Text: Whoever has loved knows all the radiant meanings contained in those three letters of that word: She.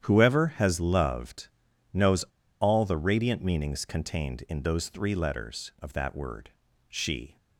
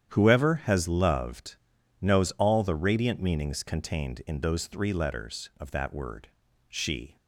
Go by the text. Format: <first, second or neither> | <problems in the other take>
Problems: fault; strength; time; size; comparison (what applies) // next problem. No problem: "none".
second | starts louder than the rest; strong; until 1.1 s; 10 dB; strong in the second // pauses between "loved" and "knows"; at 1.4 s; 0.44 s long; also in the second // pauses between "knows" and "all"; at 2.2 s; 0.36 s long